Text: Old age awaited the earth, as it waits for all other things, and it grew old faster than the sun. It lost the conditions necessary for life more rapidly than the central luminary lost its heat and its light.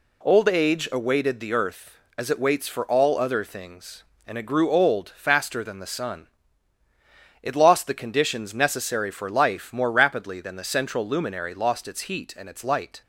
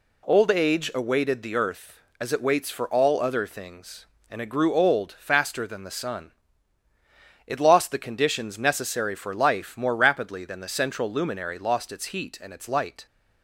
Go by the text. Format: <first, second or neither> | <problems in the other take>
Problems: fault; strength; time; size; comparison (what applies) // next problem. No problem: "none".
neither | none